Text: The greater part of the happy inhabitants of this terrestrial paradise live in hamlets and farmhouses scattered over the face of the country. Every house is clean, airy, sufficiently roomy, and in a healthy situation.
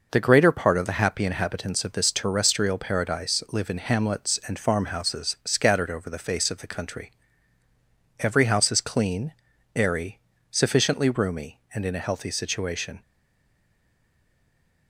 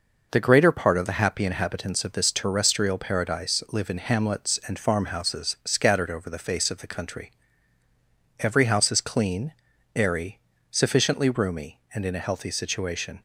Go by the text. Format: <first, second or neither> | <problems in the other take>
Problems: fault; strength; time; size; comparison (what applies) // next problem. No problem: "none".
second | stays silent after the last word; noticeable; from 13.0 s on; 1.8 s long